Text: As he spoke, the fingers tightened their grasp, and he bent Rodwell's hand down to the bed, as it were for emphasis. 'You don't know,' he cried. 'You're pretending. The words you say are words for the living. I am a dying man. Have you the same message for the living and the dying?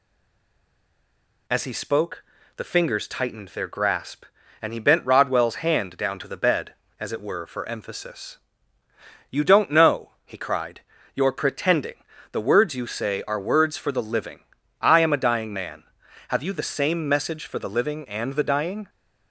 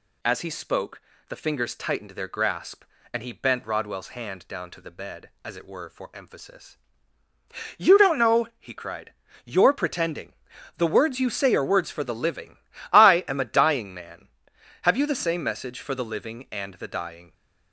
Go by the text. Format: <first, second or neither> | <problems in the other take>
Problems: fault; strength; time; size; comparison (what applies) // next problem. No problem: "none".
second | stays silent before the first word; noticeable; until 1.4 s; 1.4 s long